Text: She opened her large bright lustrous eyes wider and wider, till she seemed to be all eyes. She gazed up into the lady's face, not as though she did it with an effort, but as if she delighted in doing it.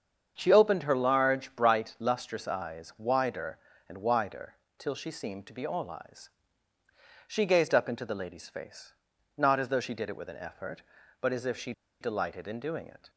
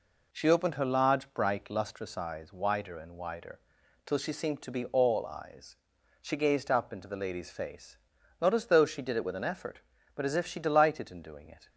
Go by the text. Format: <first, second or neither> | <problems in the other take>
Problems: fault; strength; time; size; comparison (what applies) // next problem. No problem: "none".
second | starts louder than the rest; strong; until 1.3 s; 7 dB // pauses between "she" and "delighted"; slight; at 11.7 s; 0.29 s long